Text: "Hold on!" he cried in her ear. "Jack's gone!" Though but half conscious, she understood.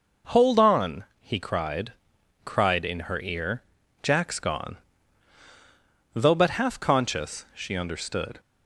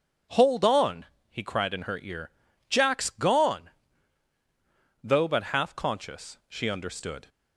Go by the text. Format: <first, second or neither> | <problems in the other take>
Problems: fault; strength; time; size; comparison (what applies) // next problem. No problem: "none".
second | says "cried" twice; at 2.4 s